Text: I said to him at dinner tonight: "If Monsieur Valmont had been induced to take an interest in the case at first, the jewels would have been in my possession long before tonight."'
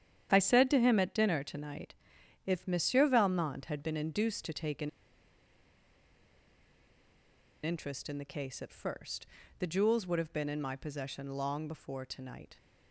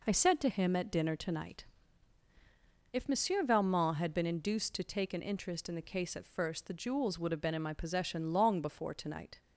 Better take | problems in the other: second | starts louder than the rest; strong; until 1.3 s; 9 dB // pauses between "an" and "interest"; strong; at 4.8 s; 2.7 s long

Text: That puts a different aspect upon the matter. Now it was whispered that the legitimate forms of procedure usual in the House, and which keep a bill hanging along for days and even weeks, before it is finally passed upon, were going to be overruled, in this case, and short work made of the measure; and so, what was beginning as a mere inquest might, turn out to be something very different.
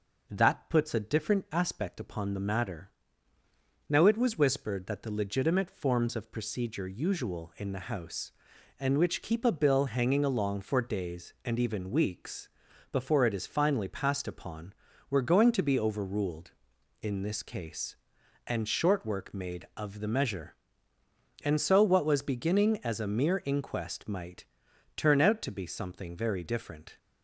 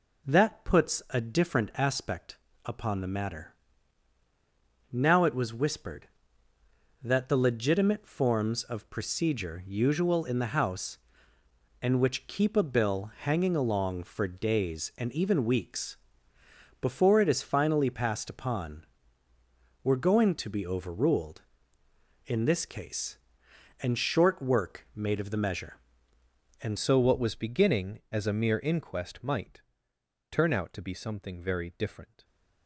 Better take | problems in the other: first | pauses between "aspect" and "upon"; slight; at 2.3 s; 0.26 s long // changes voice at "so"; from 26.7 s on; 5.5 s long

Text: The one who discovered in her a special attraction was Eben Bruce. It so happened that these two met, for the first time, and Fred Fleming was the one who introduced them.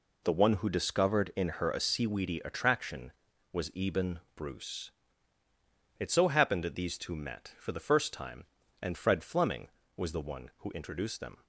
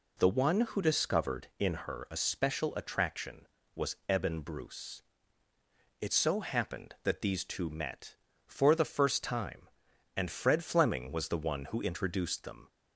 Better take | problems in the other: second | says "seaweedy" for "special"; at 1.8 s // pauses between "Eben" and "Bruce"; slight; at 4.1 s; 0.16 s long

